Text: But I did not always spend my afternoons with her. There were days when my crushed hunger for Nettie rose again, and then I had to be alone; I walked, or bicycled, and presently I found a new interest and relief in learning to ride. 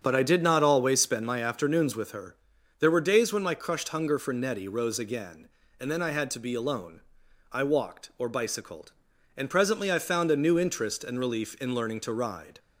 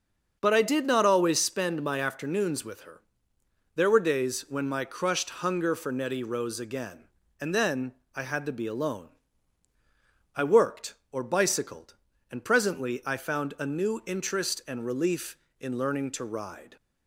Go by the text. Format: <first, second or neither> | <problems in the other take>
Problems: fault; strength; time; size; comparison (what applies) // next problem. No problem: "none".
first | starts louder than the rest; until 1.4 s; 6.5 dB; strong in the first // pauses between "then" and "I"; slight; at 7.9 s; 0.20 s long // says "worked" for "walked"; at 10.4 s